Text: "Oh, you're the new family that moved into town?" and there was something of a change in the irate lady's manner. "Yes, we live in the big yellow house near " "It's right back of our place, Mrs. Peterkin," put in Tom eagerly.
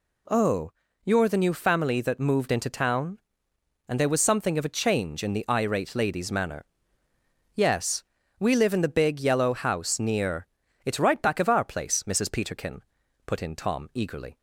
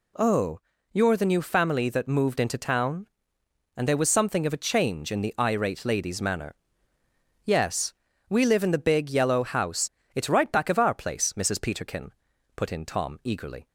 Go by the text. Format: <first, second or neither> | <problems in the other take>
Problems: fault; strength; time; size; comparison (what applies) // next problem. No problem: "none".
first | skips "near"; at 9.9 s